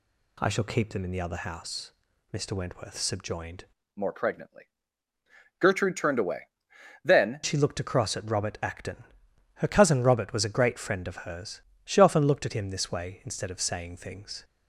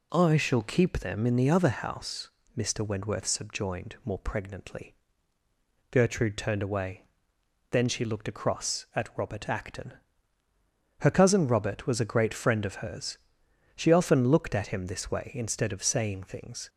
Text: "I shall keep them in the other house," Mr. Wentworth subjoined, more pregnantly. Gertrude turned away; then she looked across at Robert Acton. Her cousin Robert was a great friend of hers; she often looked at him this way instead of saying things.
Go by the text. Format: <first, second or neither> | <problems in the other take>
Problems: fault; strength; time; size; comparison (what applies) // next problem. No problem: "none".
second | changes voice from "more" to "then"; from 3.9 to 7.4 s; 3.5 s long